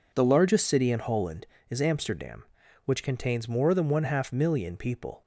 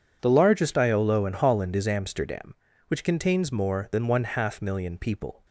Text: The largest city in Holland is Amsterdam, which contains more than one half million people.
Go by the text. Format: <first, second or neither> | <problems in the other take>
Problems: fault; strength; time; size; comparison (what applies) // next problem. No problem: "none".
first | says "iolo" for "city"; at 0.7 s